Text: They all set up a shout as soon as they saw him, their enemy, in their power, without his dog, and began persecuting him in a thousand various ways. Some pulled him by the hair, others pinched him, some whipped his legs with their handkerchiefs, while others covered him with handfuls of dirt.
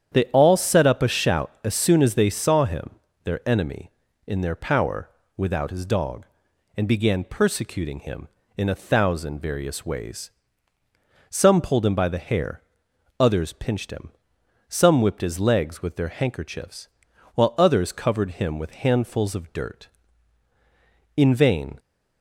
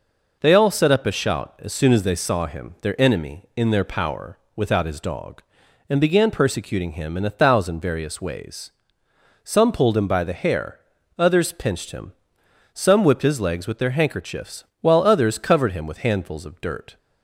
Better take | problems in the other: second | starts louder than the rest; strong; until 1.1 s; 9 dB // goes on to say "In vain"; noticeable; from 21.1 s on; 0.62 s long

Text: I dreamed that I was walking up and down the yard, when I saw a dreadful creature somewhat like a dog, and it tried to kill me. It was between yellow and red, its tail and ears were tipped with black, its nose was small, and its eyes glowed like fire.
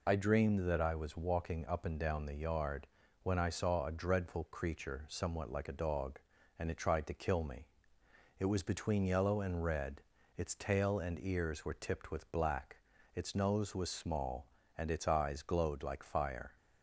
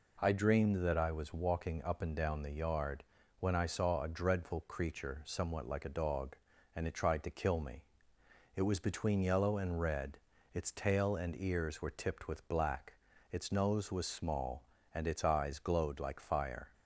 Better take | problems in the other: second | loses the start of "I"; at 0.0 s; 55 ms

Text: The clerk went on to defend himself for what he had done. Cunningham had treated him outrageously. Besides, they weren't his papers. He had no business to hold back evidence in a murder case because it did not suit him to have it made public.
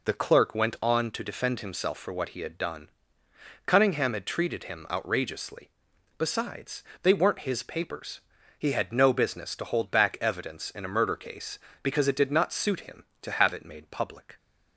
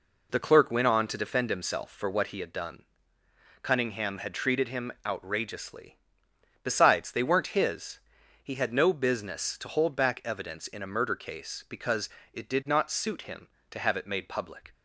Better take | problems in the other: first | skips "papers"; at 8.2 s // pauses between "because" and "it"; slight; at 12.0 s; 0.24 s long

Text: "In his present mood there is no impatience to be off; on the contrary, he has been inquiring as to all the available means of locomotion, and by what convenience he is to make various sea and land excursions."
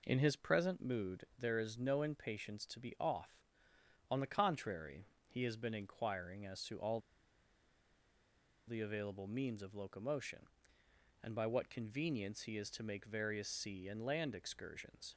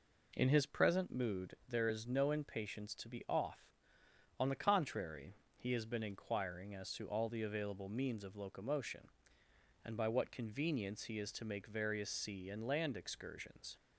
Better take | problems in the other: second | pauses between "all" and "the"; strong; at 6.9 s; 1.6 s long

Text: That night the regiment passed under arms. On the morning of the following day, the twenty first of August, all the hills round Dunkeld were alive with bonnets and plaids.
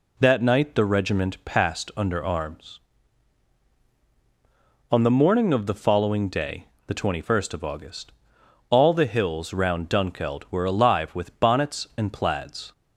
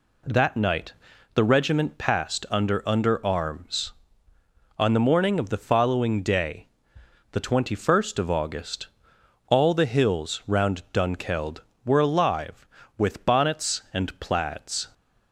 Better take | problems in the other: first | pauses between "night" and "the"; at 0.9 s; 0.40 s long // says "under" twice; at 2.8 s

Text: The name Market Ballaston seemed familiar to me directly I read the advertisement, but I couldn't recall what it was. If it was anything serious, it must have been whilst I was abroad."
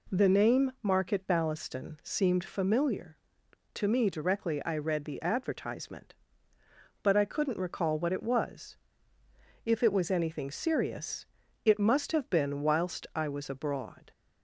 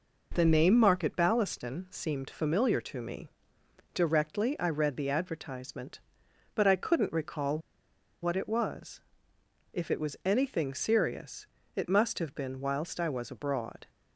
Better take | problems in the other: first | pauses between "me" and "directly"; noticeable; at 3.2 s; 0.64 s long // pauses between "recall" and "what"; noticeable; at 7.5 s; 0.63 s long

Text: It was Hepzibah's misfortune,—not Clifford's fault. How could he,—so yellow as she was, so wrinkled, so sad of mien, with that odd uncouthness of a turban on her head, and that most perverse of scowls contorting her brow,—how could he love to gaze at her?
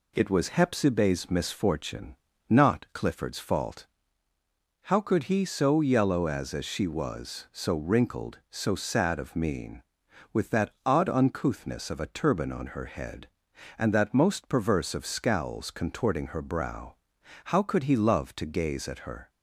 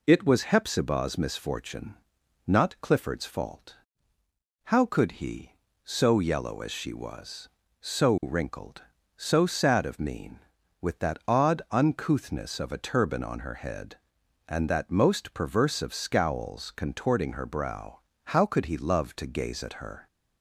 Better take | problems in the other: second | says "as" twice; at 6.5 s // pauses between "that" and "odd"; slight; at 10.6 s; 0.16 s long

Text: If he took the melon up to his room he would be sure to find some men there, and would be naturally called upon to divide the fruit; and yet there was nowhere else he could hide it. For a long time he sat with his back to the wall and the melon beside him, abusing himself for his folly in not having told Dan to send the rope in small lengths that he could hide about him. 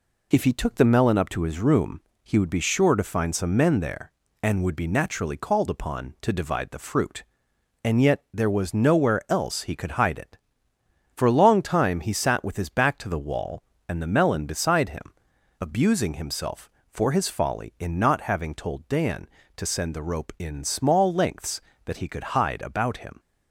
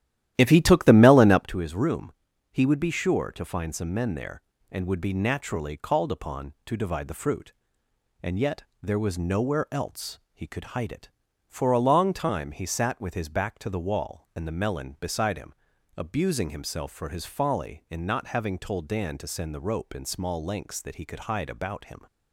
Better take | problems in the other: first | starts louder than the rest; strong; until 1.5 s; 13 dB // pauses between "room" and "he"; at 2.1 s; 0.40 s long; slight in the first // pauses between "yet" and "there"; slight; at 8.6 s; 0.18 s long

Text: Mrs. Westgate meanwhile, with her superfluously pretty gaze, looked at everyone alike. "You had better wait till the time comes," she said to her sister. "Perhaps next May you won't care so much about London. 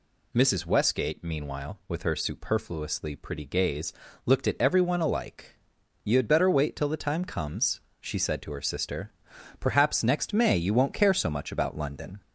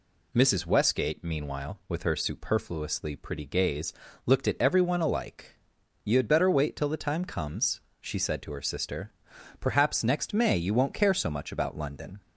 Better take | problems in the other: second | gets louder; slight; throughout; 2.5 dB

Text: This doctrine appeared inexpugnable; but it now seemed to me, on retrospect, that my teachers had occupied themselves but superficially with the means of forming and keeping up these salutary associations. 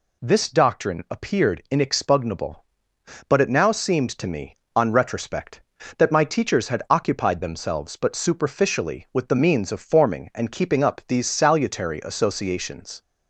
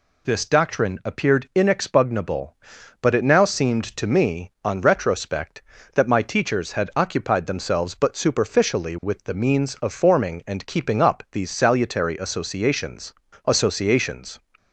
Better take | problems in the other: first | says "associations" twice; at 13.4 s

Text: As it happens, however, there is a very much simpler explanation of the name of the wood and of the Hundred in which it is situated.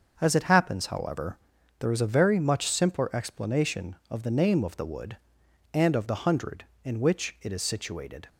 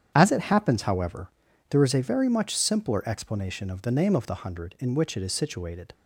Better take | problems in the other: first | starts louder than the rest; strong; until 1.1 s; 9 dB; also in the first // skips "the wood and of"; at 4.2 s

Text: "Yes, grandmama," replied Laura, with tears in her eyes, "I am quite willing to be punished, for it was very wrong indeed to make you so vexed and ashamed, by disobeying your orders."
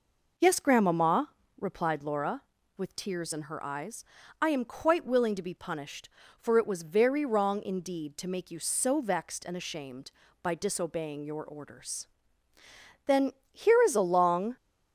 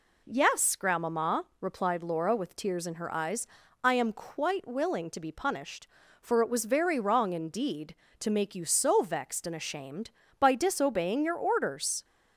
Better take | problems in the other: second | goes on to say "Then here is a long"; from 13.0 s on; 1.5 s long

